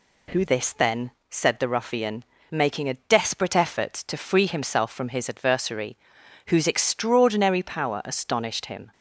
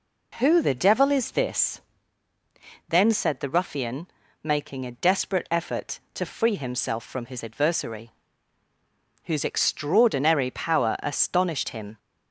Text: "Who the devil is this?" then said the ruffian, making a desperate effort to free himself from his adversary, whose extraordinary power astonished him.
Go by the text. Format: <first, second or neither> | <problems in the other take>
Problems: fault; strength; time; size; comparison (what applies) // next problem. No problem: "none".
second | skips "the devil is"; at 0.4 s // pauses between "then" and "said"; slight; at 1.1 s; 0.18 s long